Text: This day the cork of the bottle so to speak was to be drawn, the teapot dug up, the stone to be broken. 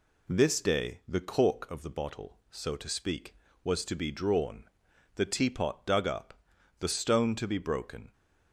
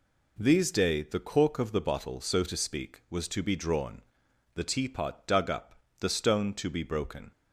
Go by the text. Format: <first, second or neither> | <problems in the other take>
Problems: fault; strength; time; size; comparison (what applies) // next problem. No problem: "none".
first | says "These" for "This"; at 0.3 s